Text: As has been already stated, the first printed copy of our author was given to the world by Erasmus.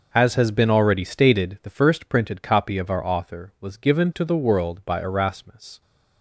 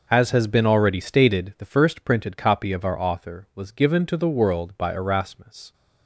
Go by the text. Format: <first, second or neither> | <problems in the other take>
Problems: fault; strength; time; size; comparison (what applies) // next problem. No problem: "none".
neither | none